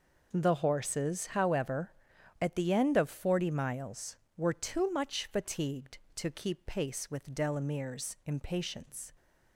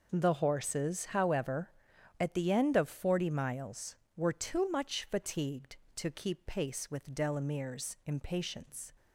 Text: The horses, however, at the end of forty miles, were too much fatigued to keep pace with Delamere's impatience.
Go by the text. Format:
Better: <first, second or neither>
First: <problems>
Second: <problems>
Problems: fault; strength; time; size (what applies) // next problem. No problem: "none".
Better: neither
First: none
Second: none